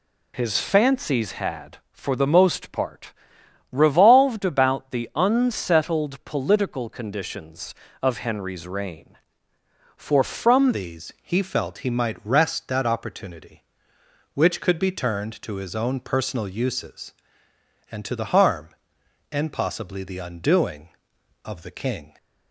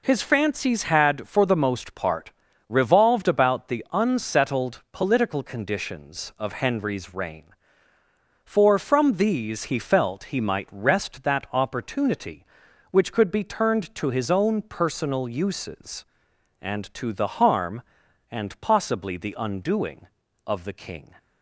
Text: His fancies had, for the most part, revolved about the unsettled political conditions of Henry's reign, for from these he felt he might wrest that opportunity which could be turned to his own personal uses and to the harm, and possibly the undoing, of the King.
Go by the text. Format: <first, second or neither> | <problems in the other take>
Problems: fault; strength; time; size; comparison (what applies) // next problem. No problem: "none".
second | changes voice at "these"; from 10.7 s on; 11.4 s long